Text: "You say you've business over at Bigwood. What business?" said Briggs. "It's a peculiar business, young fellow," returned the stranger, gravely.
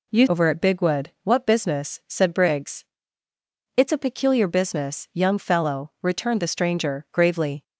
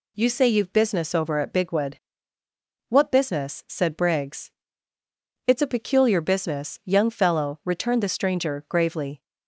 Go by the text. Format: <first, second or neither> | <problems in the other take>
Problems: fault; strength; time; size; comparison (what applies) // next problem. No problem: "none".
second | skips "say you've business"; at 0.2 s